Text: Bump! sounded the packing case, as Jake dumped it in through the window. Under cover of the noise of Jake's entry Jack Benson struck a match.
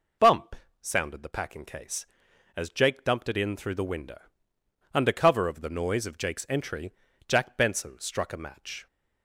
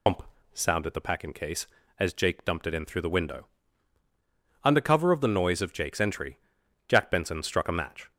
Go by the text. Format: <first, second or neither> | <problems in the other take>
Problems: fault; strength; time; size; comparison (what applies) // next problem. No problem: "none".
first | loses the start of "Bump"; at 0.0 s; 95 ms // pauses between "entry" and "Jack"; noticeable; at 6.3 s; 0.50 s long; slight in the first